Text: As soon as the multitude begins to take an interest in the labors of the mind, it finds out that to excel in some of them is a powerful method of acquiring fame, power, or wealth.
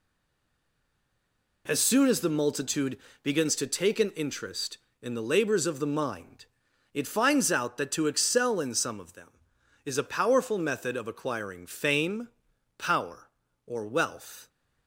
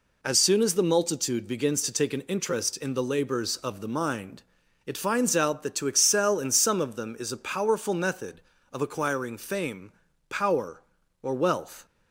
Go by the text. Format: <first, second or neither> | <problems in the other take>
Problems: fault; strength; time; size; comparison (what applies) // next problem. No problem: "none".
second | stays silent before the first word; noticeable; until 1.6 s; 1.6 s long // pauses between "multitude" and "begins"; slight; at 2.9 s; 0.28 s long